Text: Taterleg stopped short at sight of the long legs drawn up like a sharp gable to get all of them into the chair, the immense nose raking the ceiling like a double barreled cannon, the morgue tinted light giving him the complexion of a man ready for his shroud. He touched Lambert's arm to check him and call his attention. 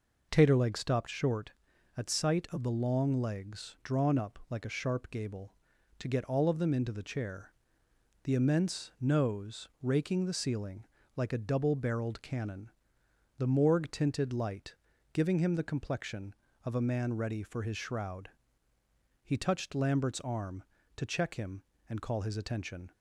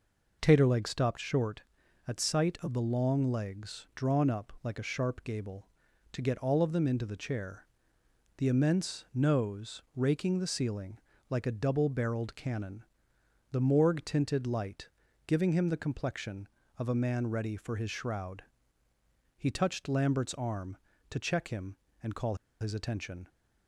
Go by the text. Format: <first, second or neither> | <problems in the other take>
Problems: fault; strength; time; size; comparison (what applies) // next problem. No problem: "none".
first | pauses between "ceiling" and "like"; slight; at 10.9 s; 0.30 s long; slight in the first // pauses between "light" and "giving"; at 14.8 s; 0.38 s long; also in the first // pauses between "call" and "his"; slight; at 22.3 s; 0.25 s long